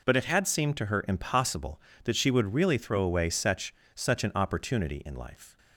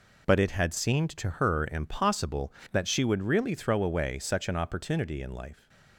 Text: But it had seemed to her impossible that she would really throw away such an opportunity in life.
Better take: second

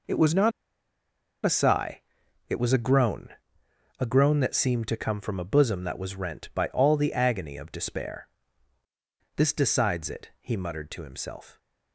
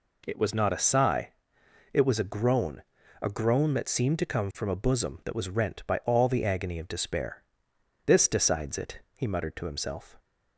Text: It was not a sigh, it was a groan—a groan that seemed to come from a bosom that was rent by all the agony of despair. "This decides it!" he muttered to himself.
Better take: second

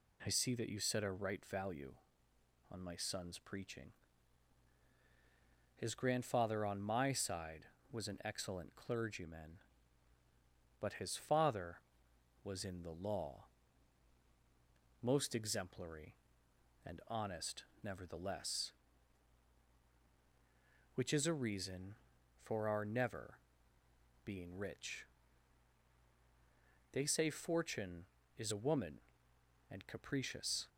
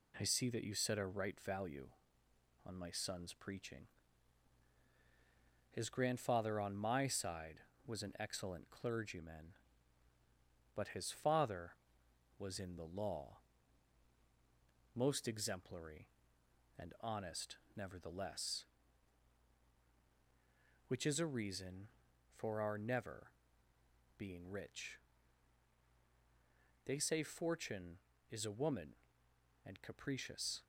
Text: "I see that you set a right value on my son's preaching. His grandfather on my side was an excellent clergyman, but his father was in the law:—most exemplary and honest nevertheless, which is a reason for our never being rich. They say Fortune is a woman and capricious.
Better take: first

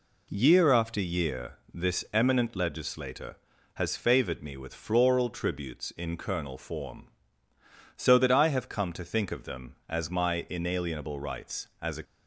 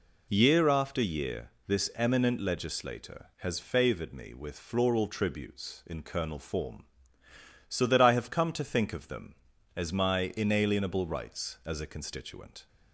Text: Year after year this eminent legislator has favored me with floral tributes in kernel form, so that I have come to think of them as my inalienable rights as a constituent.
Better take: second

